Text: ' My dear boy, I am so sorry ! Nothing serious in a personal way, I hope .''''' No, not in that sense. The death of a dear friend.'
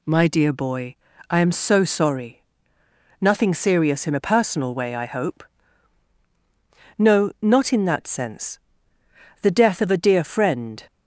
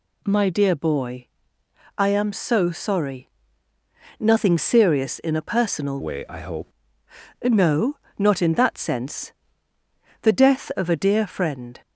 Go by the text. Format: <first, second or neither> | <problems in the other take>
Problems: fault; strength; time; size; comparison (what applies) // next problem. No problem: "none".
first | changes voice from "way" to "hope"; from 6.0 to 6.7 s; 0.7 s long